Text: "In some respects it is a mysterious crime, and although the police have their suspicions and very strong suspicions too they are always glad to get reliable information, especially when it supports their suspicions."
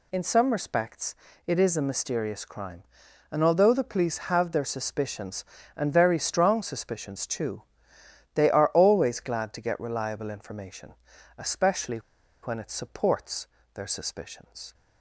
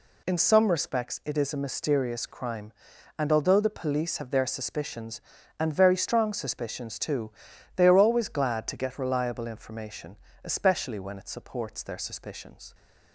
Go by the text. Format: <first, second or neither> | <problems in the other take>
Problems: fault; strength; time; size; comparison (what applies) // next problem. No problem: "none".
second | pauses between "respects" and "it"; slight; at 1.1 s; 0.30 s long // pauses between "too" and "they"; noticeable; at 7.6 s; 0.72 s long; noticeable in the second // pauses between "especially" and "when"; noticeable; at 11.9 s; 0.46 s long // pauses between "supports" and "their"; slight; at 13.4 s; 0.26 s long